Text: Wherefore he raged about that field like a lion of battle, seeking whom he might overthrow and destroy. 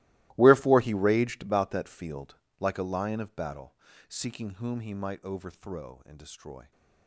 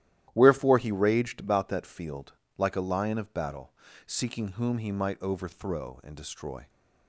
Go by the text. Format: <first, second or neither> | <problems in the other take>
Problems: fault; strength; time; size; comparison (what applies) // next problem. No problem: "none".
second | gets quieter; strong; throughout; 19 dB // starts louder than the rest; strong; until 1.3 s; 18.5 dB; strong in the second // pauses between "field" and "like"; slight; at 2.3 s; 0.24 s long; slight in the second